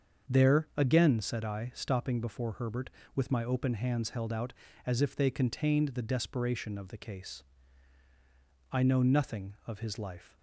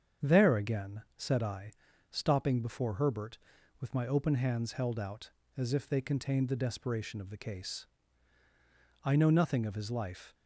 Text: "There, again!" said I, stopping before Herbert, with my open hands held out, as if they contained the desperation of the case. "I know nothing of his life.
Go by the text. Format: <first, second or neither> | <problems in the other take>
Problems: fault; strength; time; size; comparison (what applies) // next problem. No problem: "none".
neither | starts louder than the rest; the same in both